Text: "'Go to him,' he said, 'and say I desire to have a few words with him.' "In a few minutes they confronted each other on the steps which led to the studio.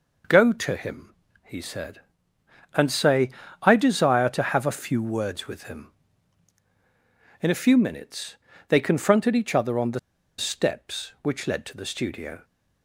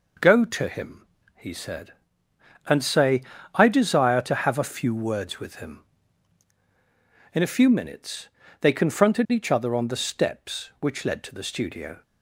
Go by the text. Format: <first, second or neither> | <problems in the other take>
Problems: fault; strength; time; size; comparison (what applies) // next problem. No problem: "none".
second | pauses between "say" and "I"; slight; at 3.2 s; 0.32 s long; slight in the second // pauses between "minutes" and "they"; slight; at 8.3 s; 0.34 s long; slight in the second // pauses between "the" and "steps"; at 9.9 s; 0.38 s long